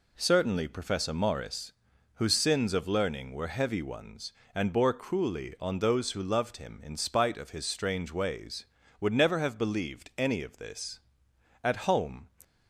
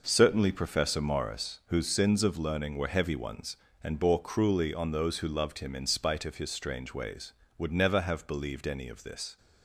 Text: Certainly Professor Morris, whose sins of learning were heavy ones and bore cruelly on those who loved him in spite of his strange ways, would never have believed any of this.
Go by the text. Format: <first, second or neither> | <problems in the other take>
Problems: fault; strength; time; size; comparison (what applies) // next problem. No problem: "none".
second | goes on to say "At home"; noticeable; from 11.6 s on; 0.66 s long